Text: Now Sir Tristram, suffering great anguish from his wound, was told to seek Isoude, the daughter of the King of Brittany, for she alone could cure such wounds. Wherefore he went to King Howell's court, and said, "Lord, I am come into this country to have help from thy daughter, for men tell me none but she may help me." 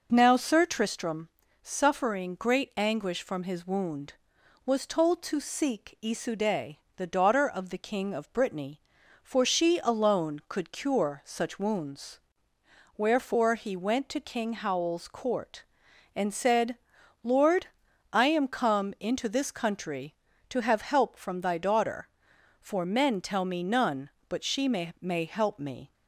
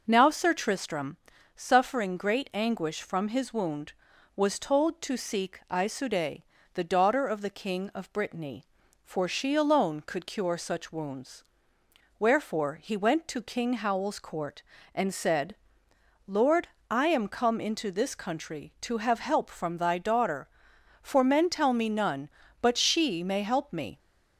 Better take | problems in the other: second | says "may" twice; at 24.9 s

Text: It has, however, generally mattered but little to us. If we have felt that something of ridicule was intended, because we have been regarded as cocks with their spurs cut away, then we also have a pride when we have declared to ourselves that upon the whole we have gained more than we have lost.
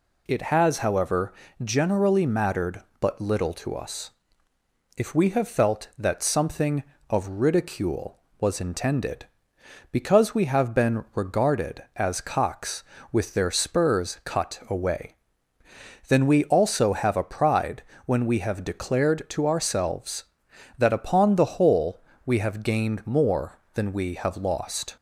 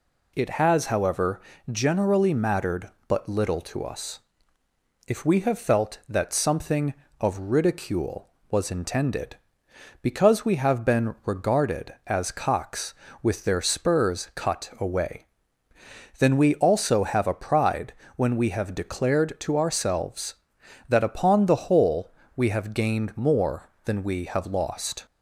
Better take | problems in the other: neither | pauses between "pride" and "when"; slight; the same in both // pauses between "whole" and "we"; slight; the same in both

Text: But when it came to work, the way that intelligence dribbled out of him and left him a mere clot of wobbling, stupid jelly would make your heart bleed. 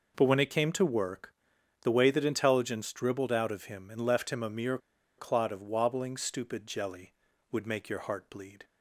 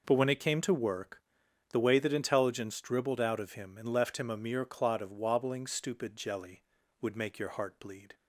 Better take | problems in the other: second | pauses between "mere" and "clot"; at 4.7 s; 0.40 s long

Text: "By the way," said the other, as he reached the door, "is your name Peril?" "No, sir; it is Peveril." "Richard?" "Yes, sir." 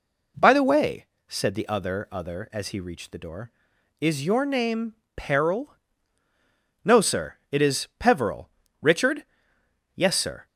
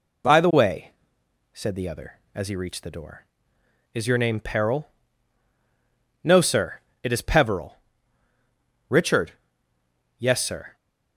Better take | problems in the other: second | says "other" twice; at 2.1 s // pauses between "name" and "Peril"; slight; at 4.9 s; 0.20 s long

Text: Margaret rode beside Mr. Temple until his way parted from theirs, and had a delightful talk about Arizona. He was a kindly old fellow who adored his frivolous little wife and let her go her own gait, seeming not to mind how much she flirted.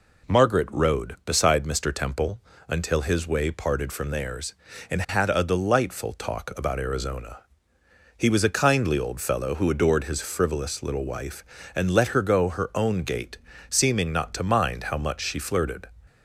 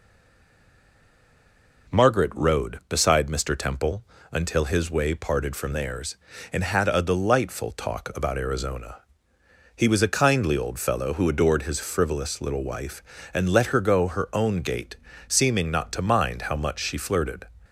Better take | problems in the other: first | stays silent before the first word; noticeable; until 1.8 s; 1.8 s long // pauses between "Temple" and "until"; slight; at 4.0 s; 0.26 s long; slight in the first

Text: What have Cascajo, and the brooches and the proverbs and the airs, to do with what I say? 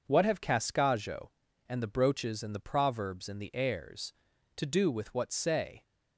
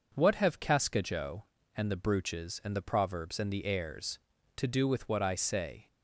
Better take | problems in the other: second | skips "I"; at 5.3 s

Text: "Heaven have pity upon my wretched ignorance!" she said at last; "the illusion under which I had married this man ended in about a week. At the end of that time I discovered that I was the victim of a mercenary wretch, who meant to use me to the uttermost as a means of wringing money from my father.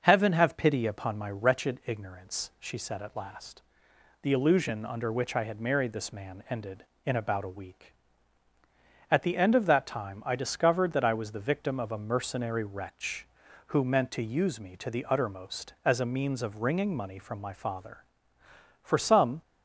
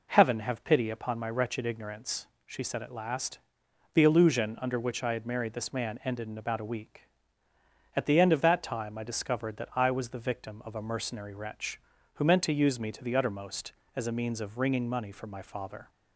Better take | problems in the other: second | starts louder than the rest; noticeable; until 1.0 s; 6 dB // goes on to say "For some"; from 18.8 s on; 0.60 s long

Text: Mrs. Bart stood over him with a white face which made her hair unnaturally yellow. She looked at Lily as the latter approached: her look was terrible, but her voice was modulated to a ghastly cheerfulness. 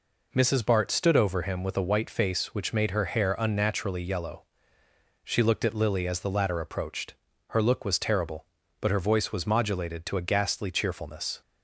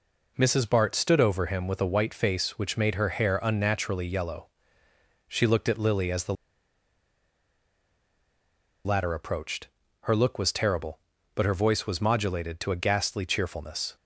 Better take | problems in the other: first | pauses between "the" and "latter"; strong; at 6.3 s; 2.5 s long

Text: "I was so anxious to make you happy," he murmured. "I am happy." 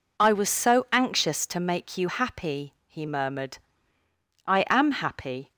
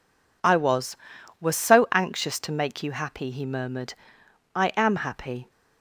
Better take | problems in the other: first | says "was" twice; at 1.3 s

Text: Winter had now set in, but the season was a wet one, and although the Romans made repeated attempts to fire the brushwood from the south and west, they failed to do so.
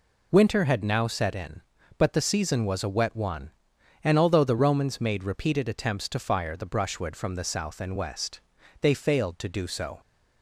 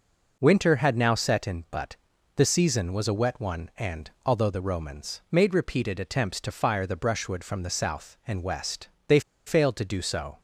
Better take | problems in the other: first | pauses between "but" and "the"; at 1.9 s; 0.40 s long // pauses between "and" and "although"; slight; at 4.0 s; 0.16 s long // pauses between "they" and "failed"; slight; at 9.1 s; 0.26 s long

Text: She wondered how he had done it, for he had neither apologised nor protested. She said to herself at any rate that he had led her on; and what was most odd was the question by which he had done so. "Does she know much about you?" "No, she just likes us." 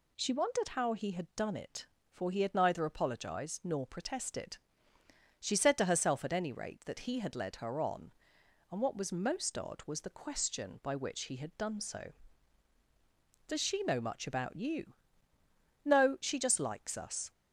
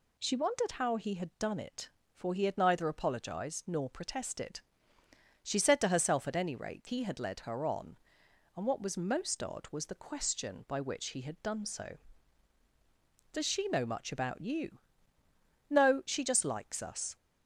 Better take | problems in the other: first | skips "that"; at 6.8 s

